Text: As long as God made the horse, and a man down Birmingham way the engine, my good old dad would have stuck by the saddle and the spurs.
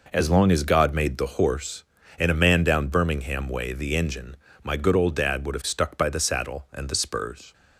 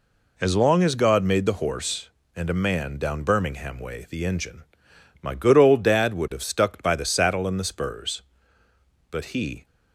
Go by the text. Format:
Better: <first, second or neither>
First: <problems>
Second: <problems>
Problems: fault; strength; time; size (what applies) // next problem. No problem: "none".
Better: first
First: none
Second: goes on to say "But he"; from 9.1 s on; 0.54 s long